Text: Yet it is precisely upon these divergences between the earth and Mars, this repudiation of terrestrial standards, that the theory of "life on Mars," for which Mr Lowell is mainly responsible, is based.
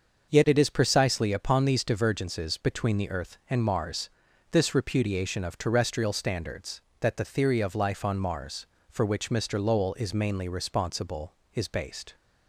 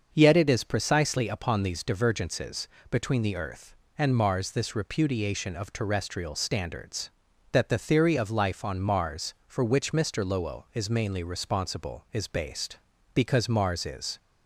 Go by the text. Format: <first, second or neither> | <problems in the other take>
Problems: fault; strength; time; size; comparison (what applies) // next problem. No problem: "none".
first | starts louder than the rest; until 1.1 s; 6.5 dB; also in the first // pauses between "divergences" and "between"; slight; at 2.6 s; 0.24 s long // goes on to say "Because Mars is"; noticeable; from 13.1 s on; 1.0 s long